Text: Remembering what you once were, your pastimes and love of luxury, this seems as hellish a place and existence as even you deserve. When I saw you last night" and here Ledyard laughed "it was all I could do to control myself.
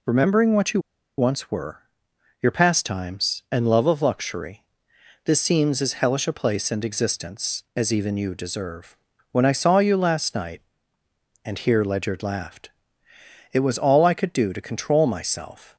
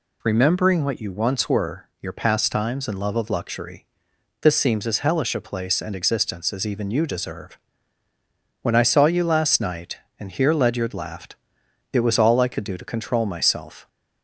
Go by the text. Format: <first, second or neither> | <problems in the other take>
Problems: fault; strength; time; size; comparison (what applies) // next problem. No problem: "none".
second | pauses between "you" and "once"; at 0.8 s; 0.37 s long // pauses between "laughed" and "it"; noticeable; at 12.6 s; 0.82 s long; noticeable in the second